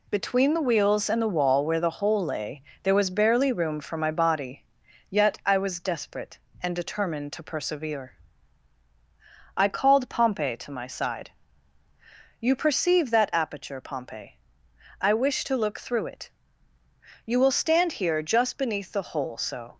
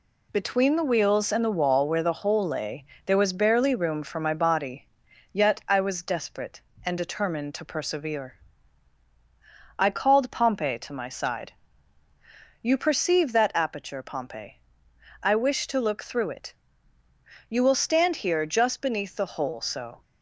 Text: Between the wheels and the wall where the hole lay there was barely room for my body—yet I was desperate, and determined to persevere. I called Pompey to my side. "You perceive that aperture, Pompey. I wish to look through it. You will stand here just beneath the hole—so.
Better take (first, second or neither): neither